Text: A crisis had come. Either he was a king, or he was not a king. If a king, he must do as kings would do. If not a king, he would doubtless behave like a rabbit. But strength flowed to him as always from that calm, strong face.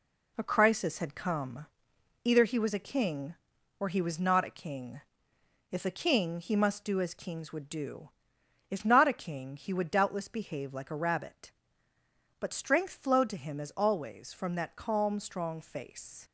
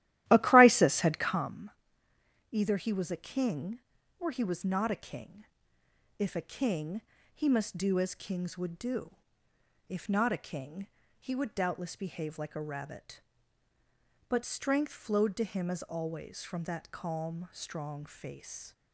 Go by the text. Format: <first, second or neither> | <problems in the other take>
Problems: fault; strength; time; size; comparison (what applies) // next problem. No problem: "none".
first | starts louder than the rest; strong; until 1.6 s; 14 dB